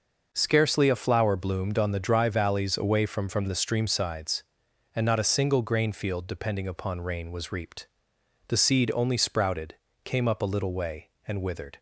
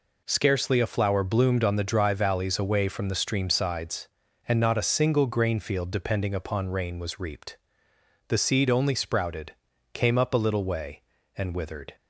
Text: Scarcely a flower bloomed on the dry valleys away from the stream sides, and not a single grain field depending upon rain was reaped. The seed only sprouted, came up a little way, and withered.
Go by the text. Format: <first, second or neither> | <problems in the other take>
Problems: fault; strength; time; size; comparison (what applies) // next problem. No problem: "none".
second | says "from" twice; at 3.2 s